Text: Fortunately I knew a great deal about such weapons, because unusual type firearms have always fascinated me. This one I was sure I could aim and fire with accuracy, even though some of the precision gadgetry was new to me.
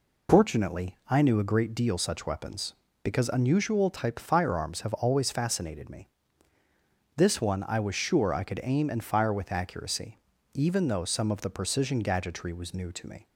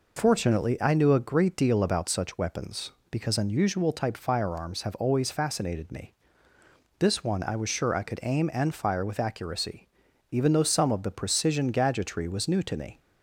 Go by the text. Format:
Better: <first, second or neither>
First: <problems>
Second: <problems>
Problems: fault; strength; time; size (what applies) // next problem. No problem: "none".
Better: second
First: skips "about"; at 1.9 s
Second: none